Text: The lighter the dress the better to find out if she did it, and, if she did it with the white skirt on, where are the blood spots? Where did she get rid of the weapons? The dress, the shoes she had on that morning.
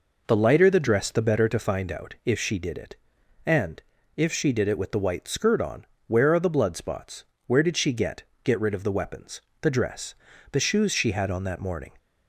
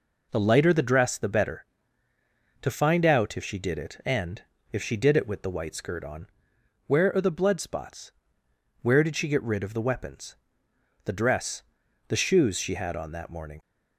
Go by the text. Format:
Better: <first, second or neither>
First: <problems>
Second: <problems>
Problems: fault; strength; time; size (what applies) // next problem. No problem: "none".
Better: second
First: says "get" twice; at 8.4 s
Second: none